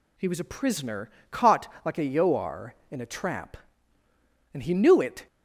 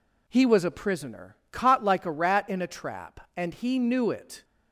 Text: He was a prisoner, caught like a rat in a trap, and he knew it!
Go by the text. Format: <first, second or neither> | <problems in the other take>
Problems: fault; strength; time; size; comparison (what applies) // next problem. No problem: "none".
second | pauses between "caught" and "like"; slight; at 1.6 s; 0.16 s long // says "yoar" for "rat"; at 2.0 s